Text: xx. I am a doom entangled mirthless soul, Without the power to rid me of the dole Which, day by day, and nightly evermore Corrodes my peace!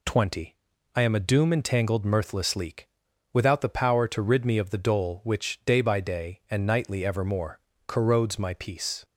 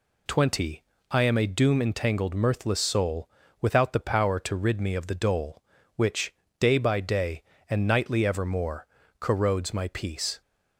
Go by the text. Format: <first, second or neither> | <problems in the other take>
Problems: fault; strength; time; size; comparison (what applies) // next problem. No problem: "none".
second | says "leak" for "soul"; at 2.5 s // pauses between "evermore" and "Corrodes"; slight; at 7.6 s; 0.26 s long; slight in the second